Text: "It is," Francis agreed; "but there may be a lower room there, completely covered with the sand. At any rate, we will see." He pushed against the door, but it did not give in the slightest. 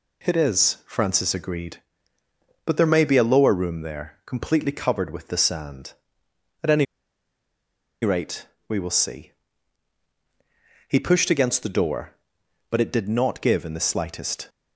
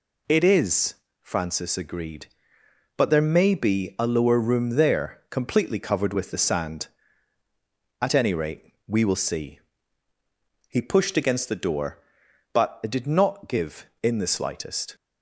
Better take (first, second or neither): second